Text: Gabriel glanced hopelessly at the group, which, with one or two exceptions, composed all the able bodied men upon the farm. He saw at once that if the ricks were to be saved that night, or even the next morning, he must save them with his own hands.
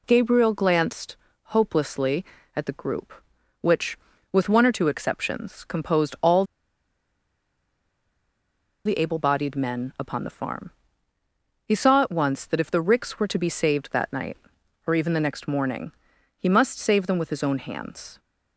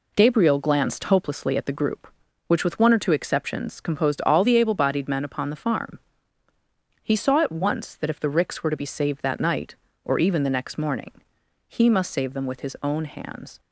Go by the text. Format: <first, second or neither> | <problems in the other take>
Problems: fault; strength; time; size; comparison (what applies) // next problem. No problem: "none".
second | pauses between "glanced" and "hopelessly"; slight; at 1.1 s; 0.32 s long // pauses between "all" and "the"; strong; at 6.4 s; 2.4 s long